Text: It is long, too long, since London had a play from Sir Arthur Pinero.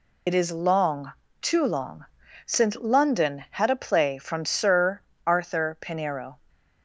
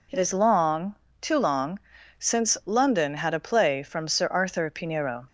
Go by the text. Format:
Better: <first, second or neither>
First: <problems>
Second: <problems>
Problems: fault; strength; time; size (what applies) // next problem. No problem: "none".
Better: second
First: loses the start of "It"; at 0.2 s; 40 ms // pauses between "Sir" and "Arthur"; slight; at 5.0 s; 0.26 s long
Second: none